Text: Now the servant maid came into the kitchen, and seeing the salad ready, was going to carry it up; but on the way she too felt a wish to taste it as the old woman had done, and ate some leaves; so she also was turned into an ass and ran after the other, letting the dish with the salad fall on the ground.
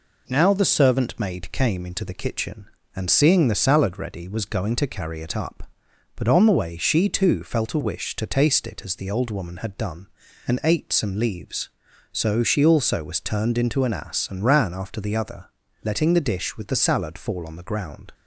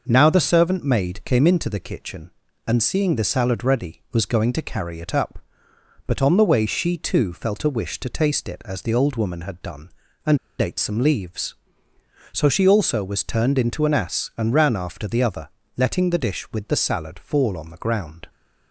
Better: first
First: none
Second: pauses between "and" and "ate"; slight; at 10.3 s; 0.21 s long

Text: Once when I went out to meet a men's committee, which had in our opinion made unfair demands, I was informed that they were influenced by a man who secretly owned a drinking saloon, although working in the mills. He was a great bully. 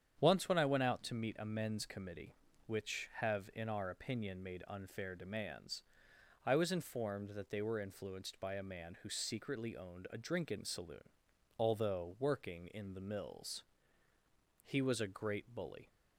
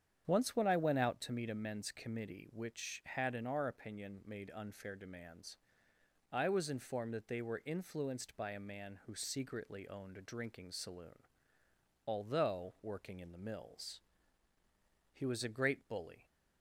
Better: second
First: starts louder than the rest; strong; until 1.2 s; 8.5 dB // says "have" for "had"; at 3.1 s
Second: starts louder than the rest; strong; until 1.2 s; 8.5 dB

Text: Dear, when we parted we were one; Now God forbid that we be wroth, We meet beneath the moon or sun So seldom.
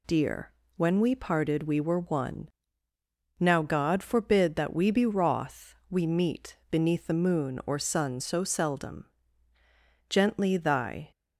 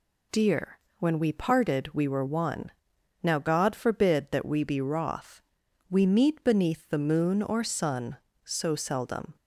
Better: second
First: goes on to say "Gently thy"; noticeable; from 10.0 s on; 1.0 s long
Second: none

